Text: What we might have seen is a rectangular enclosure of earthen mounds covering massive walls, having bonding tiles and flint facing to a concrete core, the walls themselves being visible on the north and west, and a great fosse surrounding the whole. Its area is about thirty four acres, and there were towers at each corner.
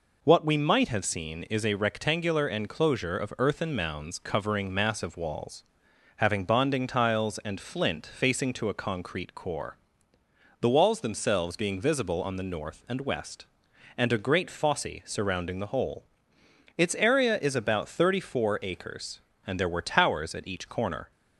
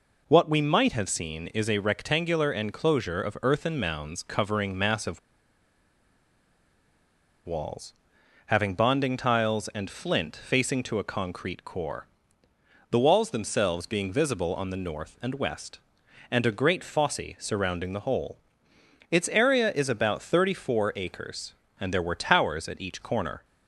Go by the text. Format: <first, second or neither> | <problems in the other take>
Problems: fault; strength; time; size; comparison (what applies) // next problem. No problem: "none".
first | pauses between "massive" and "walls"; strong; at 5.1 s; 2.2 s long // pauses between "fosse" and "surrounding"; slight; at 17.2 s; 0.18 s long; slight in the first